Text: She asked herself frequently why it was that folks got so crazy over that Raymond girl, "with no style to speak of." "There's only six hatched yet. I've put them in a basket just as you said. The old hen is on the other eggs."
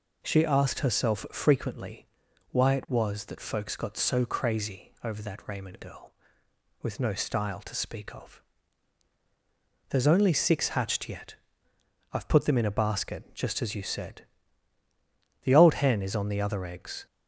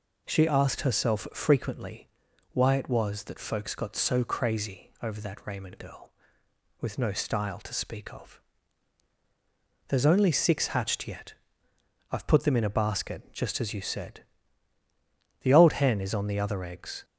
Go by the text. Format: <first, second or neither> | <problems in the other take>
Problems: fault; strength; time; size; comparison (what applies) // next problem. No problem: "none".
neither | pauses between "frequently" and "why"; the same in both